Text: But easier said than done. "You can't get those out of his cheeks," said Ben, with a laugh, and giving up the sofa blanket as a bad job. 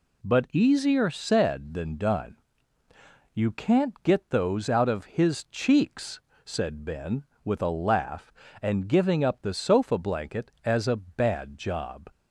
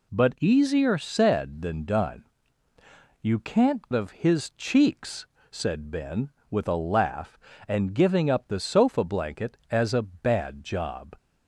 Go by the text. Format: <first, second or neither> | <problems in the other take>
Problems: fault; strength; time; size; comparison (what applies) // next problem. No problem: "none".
first | skips "get those out"; at 3.9 s